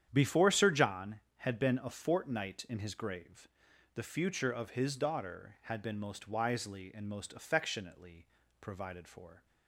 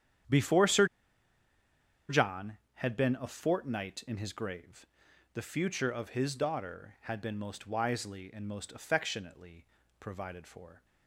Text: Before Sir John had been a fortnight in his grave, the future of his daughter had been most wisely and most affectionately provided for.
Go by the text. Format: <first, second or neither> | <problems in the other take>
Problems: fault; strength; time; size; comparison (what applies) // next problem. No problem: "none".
first | starts louder than the rest; strong; until 2.5 s; 9 dB; strong in the first // pauses between "Sir" and "John"; at 0.8 s; 1.2 s long // pauses between "affectionately" and "provided"; slight; at 9.6 s; 0.32 s long; slight in the first